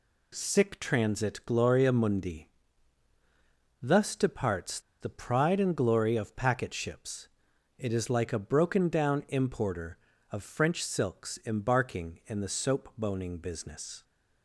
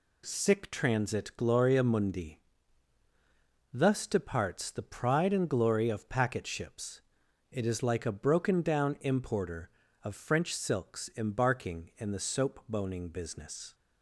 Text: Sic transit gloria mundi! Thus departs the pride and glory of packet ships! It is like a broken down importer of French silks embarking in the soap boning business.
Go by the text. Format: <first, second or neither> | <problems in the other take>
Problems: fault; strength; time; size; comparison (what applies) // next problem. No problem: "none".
second | pauses between "departs" and "the"; slight; at 4.7 s; 0.21 s long